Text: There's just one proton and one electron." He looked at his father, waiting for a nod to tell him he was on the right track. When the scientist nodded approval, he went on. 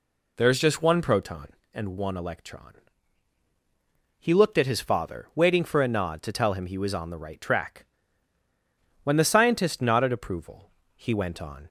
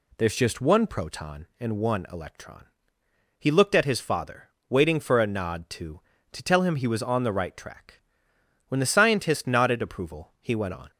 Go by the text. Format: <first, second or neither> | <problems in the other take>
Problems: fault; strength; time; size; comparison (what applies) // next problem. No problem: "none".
first | says "to" twice; at 6.3 s